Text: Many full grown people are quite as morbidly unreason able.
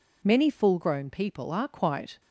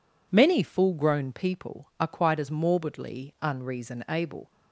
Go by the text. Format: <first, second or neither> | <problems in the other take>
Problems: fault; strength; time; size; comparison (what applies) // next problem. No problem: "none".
second | stops before "as morbidly unreason able"; at 2.1 s